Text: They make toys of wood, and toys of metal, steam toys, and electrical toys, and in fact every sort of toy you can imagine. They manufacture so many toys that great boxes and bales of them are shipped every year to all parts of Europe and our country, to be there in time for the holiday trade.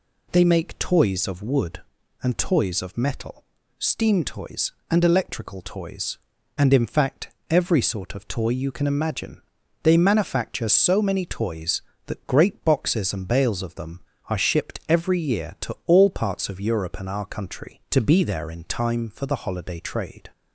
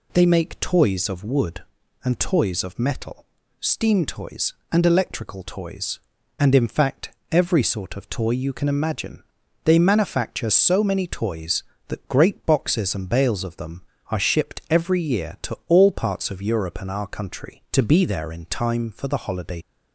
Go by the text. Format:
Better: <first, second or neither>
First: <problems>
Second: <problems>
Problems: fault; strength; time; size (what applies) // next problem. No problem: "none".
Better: first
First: pauses between "fact" and "every"; slight; at 7.3 s; 0.18 s long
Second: pauses between "fact" and "every"; slight; at 7.1 s; 0.18 s long // stops before "trade"; at 19.6 s